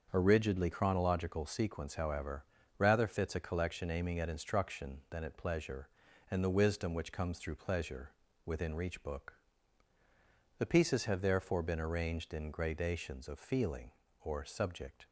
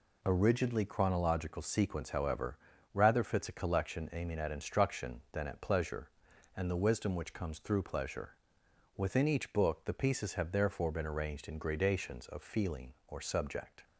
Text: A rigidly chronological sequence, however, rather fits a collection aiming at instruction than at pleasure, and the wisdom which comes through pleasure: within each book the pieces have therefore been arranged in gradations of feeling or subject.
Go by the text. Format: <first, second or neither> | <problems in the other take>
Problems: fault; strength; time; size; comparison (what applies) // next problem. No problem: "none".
second | starts louder than the rest; until 1.1 s; 6.5 dB // says "reach" for "each"; at 8.7 s // pauses between "book" and "the"; at 9.3 s; 1.2 s long